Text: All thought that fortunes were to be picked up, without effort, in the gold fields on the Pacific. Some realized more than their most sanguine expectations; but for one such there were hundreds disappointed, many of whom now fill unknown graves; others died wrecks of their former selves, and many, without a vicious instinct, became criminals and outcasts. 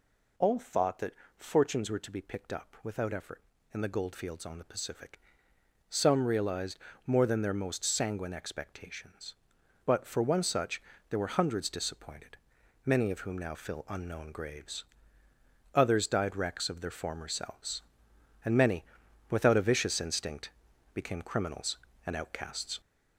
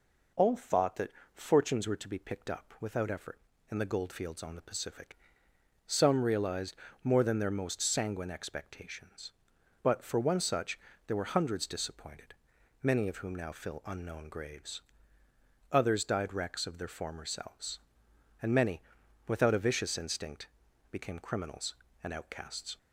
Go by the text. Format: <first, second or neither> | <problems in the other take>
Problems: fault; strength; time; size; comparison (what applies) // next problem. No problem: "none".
second | gets louder; throughout; 3.5 dB // pauses between "that" and "fortunes"; slight; at 1.1 s; 0.24 s long; slight in the second // pauses between "realized" and "more"; slight; at 6.7 s; 0.28 s long; slight in the second // pauses between "such" and "there"; slight; at 10.8 s; 0.26 s long; slight in the second